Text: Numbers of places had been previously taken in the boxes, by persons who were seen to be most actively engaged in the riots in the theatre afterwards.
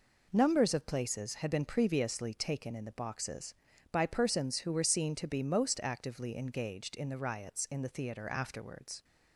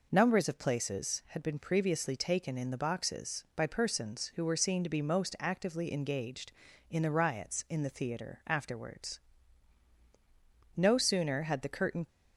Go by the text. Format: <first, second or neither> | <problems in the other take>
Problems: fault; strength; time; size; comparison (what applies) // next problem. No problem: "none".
first | goes on to say "No sooner had the curtain"; from 10.7 s on; 1.3 s long